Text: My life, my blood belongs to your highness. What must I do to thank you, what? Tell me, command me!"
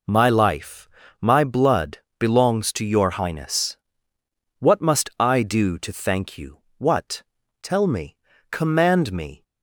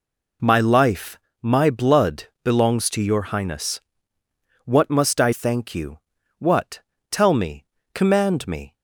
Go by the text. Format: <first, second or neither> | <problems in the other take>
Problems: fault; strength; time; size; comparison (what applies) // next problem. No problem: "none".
first | pauses between "blood" and "belongs"; slight; at 2.2 s; 0.20 s long; slight in the first // skips "do to"; at 5.3 s